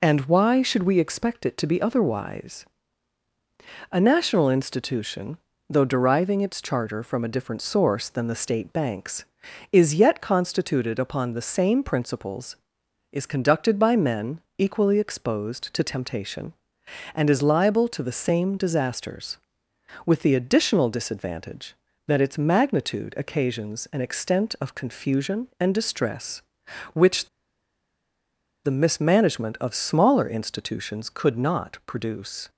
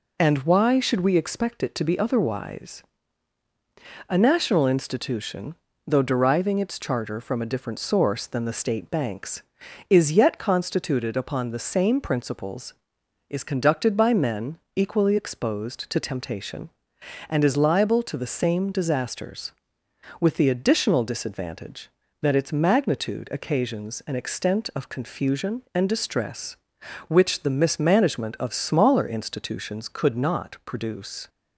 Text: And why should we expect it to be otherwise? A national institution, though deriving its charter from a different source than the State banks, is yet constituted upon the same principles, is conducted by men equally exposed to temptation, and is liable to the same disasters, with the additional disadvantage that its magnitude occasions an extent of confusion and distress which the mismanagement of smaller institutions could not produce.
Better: second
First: pauses between "men" and "equally"; slight; at 14.4 s; 0.16 s long // pauses between "which" and "the"; strong; at 27.2 s; 1.3 s long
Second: pauses between "men" and "equally"; slight; at 14.5 s; 0.16 s long

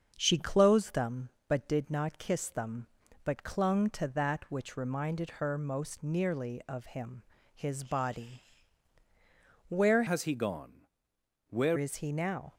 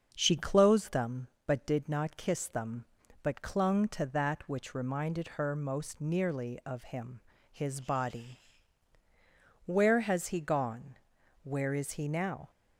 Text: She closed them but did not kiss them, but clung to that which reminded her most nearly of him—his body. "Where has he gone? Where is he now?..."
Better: second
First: starts louder than the rest; until 1.1 s; 7 dB // changes voice from "has" to "Where"; from 10.0 to 11.7 s; 1.7 s long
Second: starts louder than the rest; until 1.1 s; 7 dB

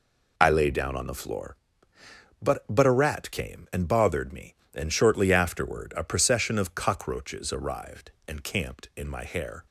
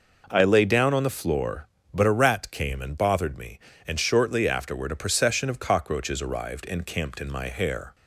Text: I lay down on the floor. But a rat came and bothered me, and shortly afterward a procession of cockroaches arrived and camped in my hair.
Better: second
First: says "But" twice; at 2.6 s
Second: none

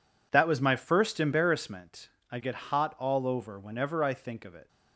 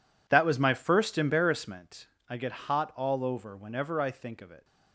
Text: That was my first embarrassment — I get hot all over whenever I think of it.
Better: first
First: none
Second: gets quieter; strong; throughout; 15 dB

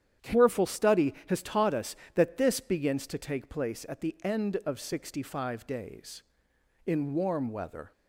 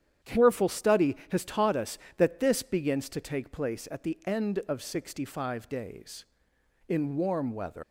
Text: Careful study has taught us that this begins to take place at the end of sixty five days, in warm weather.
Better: first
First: starts louder than the rest; strong; until 1.3 s; 9.5 dB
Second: starts louder than the rest; strong; until 1.3 s; 9.5 dB // leaves "weather" unfinished; at 7.8 s; 110 ms

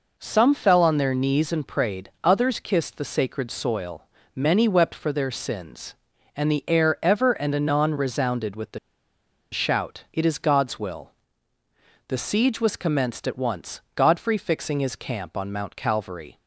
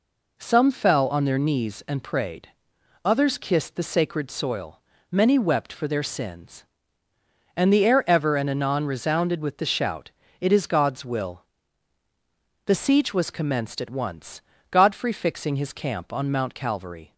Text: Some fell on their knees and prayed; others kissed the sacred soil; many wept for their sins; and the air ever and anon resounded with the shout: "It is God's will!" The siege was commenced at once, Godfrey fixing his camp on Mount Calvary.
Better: second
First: pauses between "the" and "shout"; noticeable; at 8.7 s; 0.73 s long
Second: none

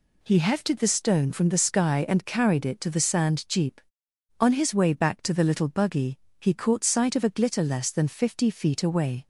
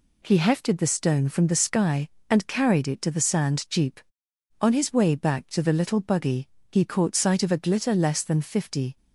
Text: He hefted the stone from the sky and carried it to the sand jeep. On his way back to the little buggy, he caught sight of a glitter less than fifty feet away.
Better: first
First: none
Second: stops before "feet away"; at 8.9 s

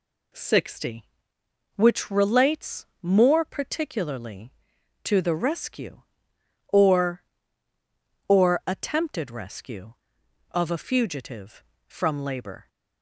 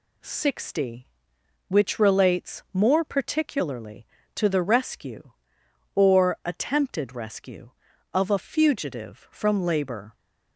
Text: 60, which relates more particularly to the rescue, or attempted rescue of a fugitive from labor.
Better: second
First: pauses between "relates" and "more"; slight; at 2.8 s; 0.16 s long // says "or" twice; at 8.2 s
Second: none

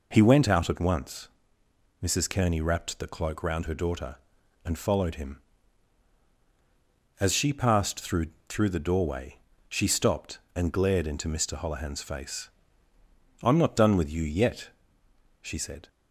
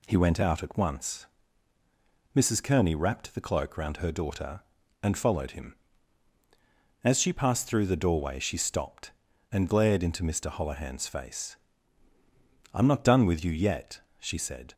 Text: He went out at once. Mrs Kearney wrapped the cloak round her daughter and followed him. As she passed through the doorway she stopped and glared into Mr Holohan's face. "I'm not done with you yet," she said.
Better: second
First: says "through" twice; at 8.4 s // pauses between "doorway" and "she"; slight; at 9.3 s; 0.32 s long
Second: none

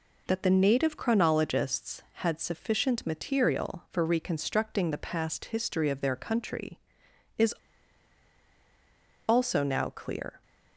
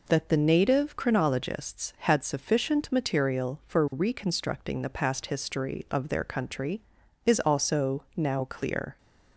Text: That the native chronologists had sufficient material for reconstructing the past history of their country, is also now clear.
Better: second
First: pauses between "is" and "also"; strong; at 7.5 s; 1.7 s long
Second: none

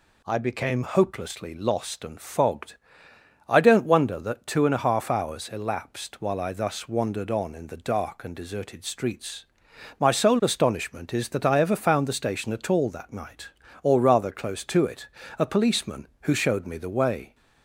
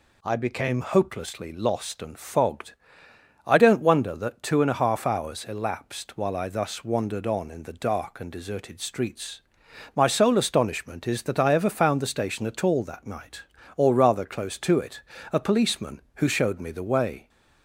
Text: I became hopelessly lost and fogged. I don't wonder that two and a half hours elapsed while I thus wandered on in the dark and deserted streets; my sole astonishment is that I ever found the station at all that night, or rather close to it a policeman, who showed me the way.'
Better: neither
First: pauses between "it" and "a"; slight; at 15.0 s; 0.28 s long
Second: pauses between "it" and "a"; slight; at 15.0 s; 0.28 s long

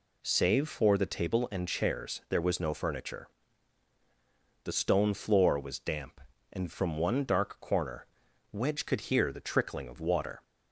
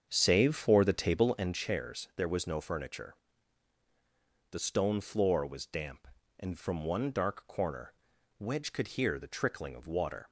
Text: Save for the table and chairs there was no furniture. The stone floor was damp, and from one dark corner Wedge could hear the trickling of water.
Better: first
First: pauses between "corner" and "Wedge"; noticeable; at 8.0 s; 0.46 s long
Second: starts louder than the rest; strong; until 1.6 s; 7 dB // pauses between "corner" and "Wedge"; noticeable; at 7.9 s; 0.46 s long

